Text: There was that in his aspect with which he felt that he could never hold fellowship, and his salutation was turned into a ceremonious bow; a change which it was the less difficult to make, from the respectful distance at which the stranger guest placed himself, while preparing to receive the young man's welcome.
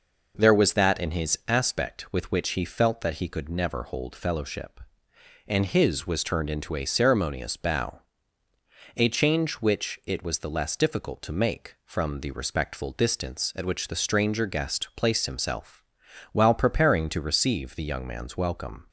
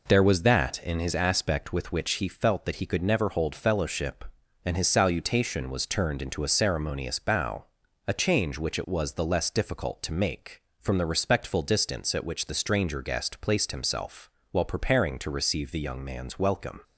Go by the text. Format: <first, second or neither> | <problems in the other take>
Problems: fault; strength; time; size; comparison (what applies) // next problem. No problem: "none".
second | skips "salutation"; at 6.0 s